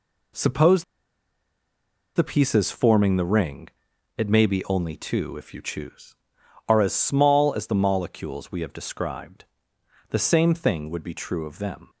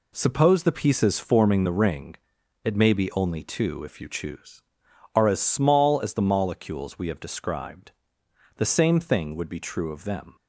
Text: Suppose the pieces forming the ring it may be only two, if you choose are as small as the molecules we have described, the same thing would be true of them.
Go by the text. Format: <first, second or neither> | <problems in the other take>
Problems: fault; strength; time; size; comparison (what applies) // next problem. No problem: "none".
second | pauses between "Suppose" and "the"; strong; at 0.8 s; 1.3 s long // pauses between "ring" and "it"; noticeable; at 3.6 s; 0.46 s long; noticeable in the second